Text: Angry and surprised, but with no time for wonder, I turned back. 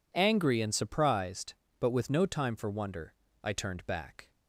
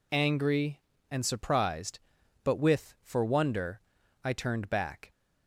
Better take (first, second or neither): first